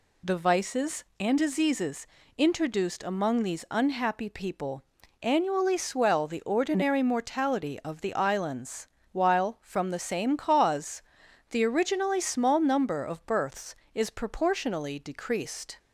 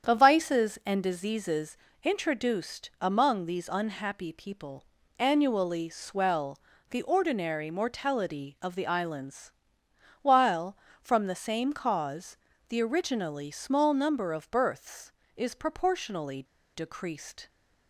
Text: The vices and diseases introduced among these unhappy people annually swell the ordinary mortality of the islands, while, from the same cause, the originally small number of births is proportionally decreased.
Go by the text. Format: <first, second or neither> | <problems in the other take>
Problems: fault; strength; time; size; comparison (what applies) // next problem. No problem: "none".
first | starts louder than the rest; strong; until 1.1 s; 8 dB // pauses between "diseases" and "introduced"; slight; at 1.7 s; 0.24 s long; slight in the first // pauses between "people" and "annually"; slight; at 4.8 s; 0.34 s long; also in the first // pauses between "swell" and "the"; slight; at 6.5 s; 0.32 s long // pauses between "proportionally" and "decreased"; slight; at 16.4 s; 0.32 s long